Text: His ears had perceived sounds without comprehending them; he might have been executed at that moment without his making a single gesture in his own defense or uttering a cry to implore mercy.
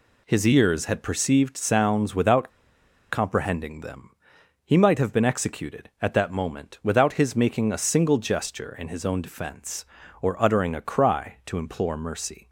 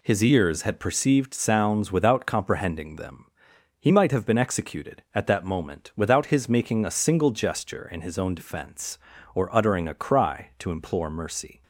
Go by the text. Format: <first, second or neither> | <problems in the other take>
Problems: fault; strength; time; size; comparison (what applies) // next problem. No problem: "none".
second | pauses between "without" and "comprehending"; noticeable; at 2.4 s; 0.64 s long